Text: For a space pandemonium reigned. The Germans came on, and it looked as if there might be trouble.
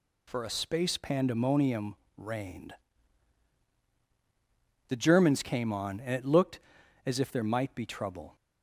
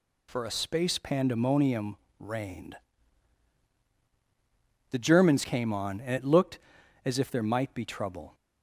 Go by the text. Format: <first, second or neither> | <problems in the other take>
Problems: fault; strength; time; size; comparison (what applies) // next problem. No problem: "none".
neither | pauses between "pandemonium" and "reigned"; slight; the same in both